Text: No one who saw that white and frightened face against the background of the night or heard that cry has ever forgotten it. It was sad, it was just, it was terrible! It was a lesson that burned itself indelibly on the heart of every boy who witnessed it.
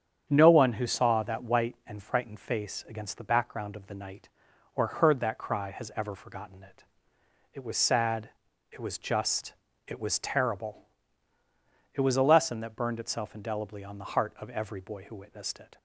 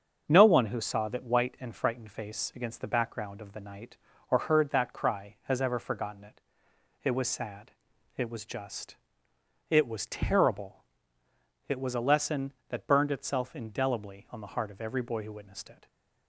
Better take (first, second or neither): neither